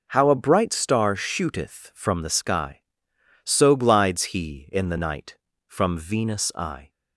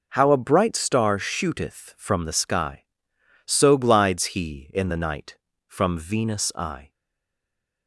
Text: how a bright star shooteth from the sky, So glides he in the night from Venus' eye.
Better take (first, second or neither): first